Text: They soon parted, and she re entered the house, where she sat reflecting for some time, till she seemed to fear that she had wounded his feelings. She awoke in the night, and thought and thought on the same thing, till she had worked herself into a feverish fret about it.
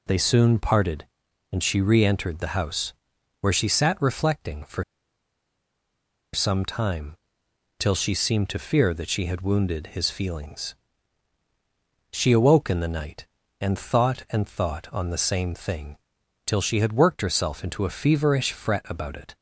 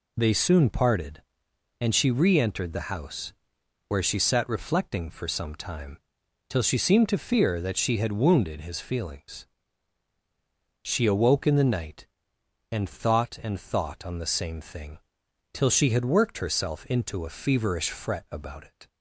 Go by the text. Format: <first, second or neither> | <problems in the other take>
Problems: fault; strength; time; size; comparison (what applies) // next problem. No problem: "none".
second | pauses between "for" and "some"; strong; at 4.8 s; 1.4 s long